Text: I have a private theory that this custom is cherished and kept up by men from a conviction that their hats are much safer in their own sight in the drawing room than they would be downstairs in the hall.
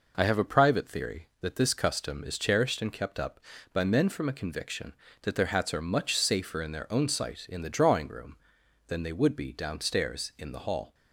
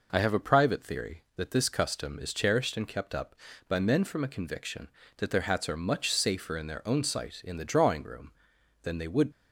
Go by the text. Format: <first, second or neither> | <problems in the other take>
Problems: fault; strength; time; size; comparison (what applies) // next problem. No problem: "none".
first | stops before "be downstairs in the hall"; at 9.3 s